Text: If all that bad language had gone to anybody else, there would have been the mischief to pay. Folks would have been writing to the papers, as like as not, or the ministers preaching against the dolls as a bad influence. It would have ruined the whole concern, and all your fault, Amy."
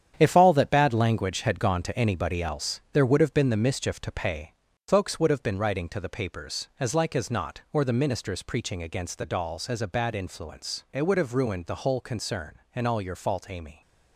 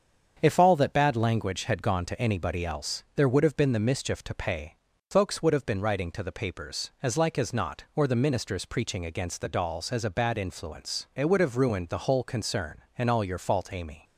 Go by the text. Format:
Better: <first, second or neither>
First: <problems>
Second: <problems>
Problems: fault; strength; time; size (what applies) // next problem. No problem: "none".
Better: second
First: gets quieter; strong; throughout; 8.5 dB // starts louder than the rest; strong; until 1.1 s; 9 dB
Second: starts louder than the rest; strong; until 1.4 s; 7.5 dB